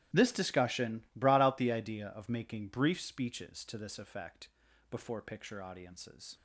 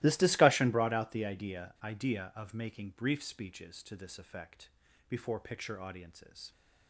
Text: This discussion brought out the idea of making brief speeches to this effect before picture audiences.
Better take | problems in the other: first | starts louder than the rest; strong; until 1.0 s; 17.5 dB; strong in the first // says "idea" twice; at 1.8 s // pauses between "effect" and "before"; at 4.6 s; 0.40 s long; also in the first

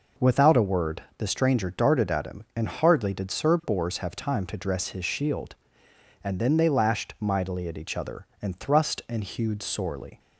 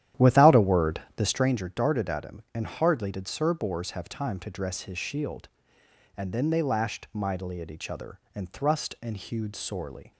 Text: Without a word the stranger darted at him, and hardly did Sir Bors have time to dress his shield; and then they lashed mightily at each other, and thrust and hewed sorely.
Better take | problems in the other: first | starts louder than the rest; strong; until 1.6 s; 11.5 dB // pauses between "word" and "the"; slight; at 1.0 s; 0.16 s long; slight in the first

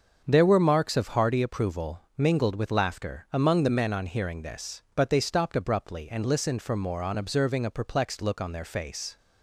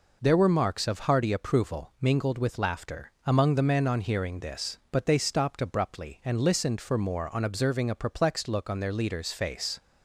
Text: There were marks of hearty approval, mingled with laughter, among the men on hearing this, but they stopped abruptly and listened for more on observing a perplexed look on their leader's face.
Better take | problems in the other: second | starts louder than the rest; until 1.2 s; 7 dB // skips "leader's"; at 8.6 s

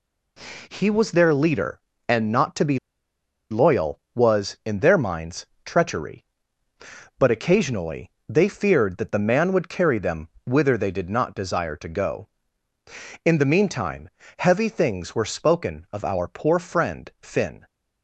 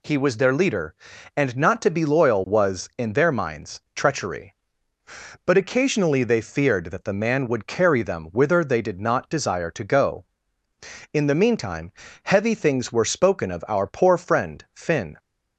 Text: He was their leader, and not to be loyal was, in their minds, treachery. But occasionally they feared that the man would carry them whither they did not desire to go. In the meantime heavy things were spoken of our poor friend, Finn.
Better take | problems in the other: second | pauses between "be" and "loyal"; noticeable; at 2.7 s; 0.73 s long // pauses between "occasionally" and "they"; slight; at 8.1 s; 0.16 s long // pauses between "them" and "whither"; slight; at 10.2 s; 0.18 s long // pauses between "meantime" and "heavy"; slight; at 14.0 s; 0.28 s long; slight in the second

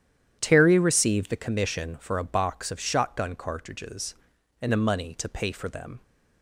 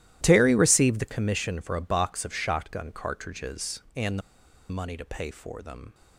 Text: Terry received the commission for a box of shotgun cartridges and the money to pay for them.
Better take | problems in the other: first | starts louder than the rest; strong; until 1.2 s; 14 dB; strong in the first // pauses between "the" and "money"; noticeable; at 4.2 s; 0.49 s long

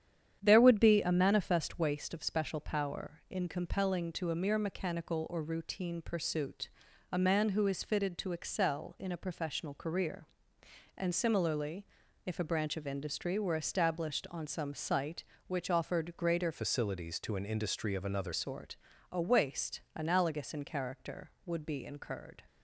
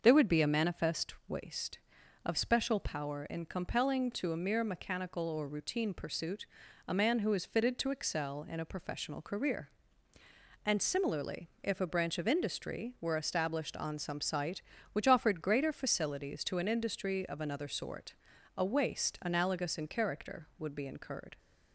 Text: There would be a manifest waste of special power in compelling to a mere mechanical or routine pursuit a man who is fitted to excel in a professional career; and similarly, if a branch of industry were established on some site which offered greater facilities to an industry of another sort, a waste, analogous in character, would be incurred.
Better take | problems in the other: second | starts louder than the rest; strong; until 1.4 s; 9 dB; also in the second // pauses between "pursuit" and "a"; at 6.6 s; 0.42 s long; also in the second // changes voice from "facilities" to "another"; from 16.5 to 18.3 s; 1.8 s long

